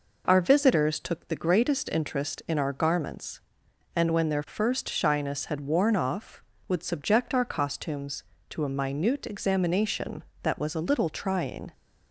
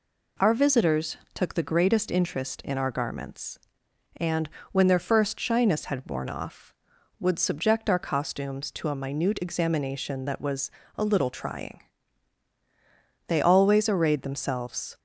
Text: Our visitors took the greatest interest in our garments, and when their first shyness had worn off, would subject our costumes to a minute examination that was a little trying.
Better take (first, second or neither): first